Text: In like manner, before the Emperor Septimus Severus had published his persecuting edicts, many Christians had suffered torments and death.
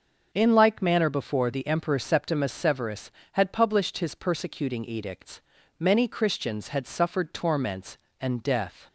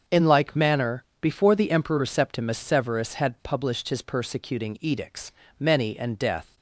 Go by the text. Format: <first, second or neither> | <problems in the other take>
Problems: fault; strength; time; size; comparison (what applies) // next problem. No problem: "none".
first | starts louder than the rest; until 1.2 s; 7 dB; noticeable in the first // skips "Christians had suffered torments"; at 5.9 s